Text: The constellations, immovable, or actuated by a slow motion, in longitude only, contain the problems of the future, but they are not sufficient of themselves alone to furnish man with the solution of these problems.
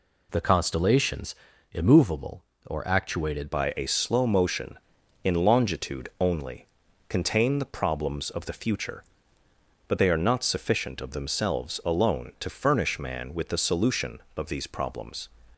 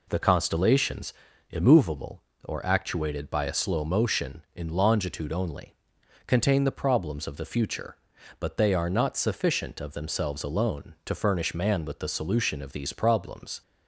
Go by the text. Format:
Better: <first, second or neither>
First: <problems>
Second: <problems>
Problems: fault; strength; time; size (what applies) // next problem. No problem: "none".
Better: second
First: changes voice at "by"; from 3.5 s on; 11.7 s long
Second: none